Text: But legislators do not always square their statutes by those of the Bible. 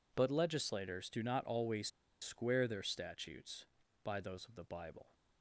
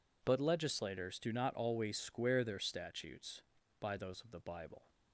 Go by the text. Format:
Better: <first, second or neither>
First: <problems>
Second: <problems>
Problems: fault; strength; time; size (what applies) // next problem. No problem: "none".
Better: second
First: pauses between "always" and "square"; slight; at 1.8 s; 0.33 s long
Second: none